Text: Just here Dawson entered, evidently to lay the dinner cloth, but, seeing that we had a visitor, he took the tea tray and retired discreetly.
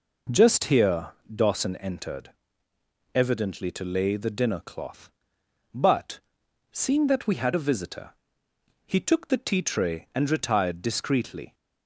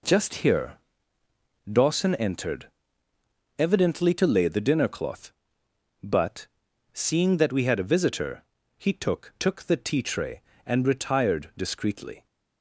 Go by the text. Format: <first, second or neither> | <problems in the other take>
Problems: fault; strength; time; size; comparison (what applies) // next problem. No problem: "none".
first | pauses between "here" and "Dawson"; noticeable; at 0.7 s; 0.96 s long; slight in the first // says "took" twice; at 9.3 s